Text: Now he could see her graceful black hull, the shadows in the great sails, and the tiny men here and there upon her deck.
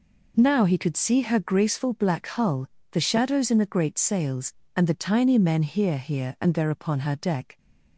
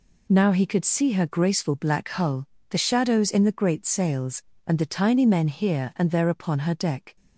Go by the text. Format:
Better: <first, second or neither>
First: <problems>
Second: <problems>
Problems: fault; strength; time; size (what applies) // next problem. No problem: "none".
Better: second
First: says "here" twice; at 5.9 s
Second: none